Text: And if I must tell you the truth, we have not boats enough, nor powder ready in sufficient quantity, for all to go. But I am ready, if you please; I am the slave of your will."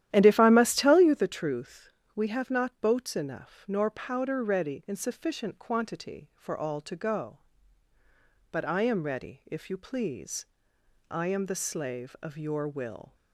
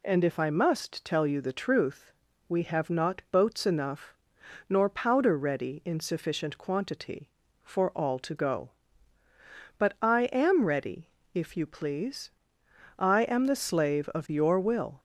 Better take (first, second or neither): second